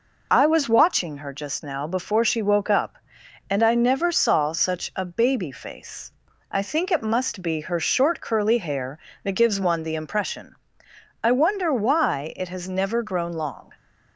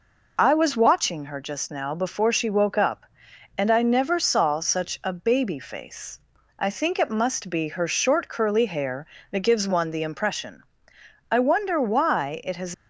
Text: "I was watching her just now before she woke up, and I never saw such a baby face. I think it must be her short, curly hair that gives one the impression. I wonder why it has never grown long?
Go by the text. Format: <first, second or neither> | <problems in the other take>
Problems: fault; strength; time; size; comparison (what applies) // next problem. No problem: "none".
first | stops before "never grown long"; at 12.7 s